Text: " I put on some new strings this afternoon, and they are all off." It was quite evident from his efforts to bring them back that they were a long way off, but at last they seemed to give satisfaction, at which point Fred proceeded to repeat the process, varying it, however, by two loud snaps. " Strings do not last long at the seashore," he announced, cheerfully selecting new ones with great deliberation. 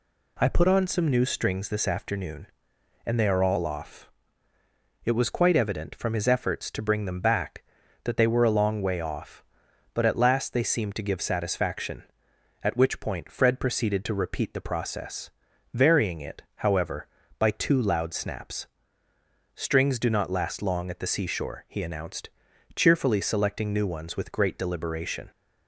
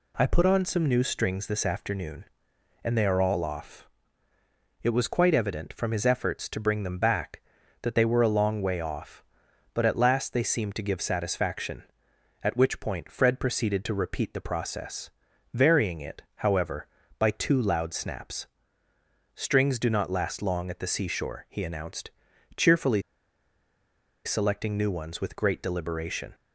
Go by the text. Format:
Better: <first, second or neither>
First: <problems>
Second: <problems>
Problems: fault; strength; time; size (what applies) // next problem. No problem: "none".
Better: first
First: none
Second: pauses between "cheerfully" and "selecting"; at 23.0 s; 1.2 s long